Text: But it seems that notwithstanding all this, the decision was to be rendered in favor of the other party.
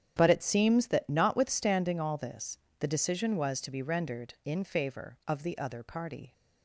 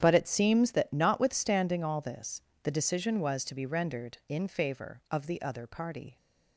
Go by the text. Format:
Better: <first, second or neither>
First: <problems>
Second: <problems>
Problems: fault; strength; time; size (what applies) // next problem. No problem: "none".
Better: neither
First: starts louder than the rest; strong; until 1.2 s; 8.5 dB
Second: starts louder than the rest; strong; until 1.0 s; 8.5 dB